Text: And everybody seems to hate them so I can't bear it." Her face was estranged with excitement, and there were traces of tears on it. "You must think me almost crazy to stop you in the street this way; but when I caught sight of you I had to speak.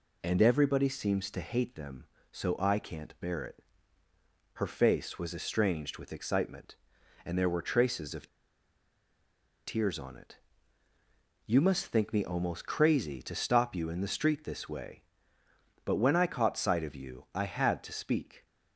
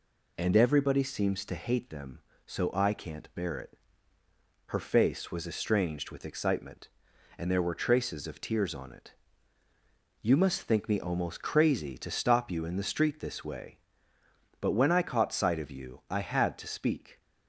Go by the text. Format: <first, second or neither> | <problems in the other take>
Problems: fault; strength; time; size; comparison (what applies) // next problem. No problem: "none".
second | pauses between "of" and "tears"; strong; at 8.2 s; 1.3 s long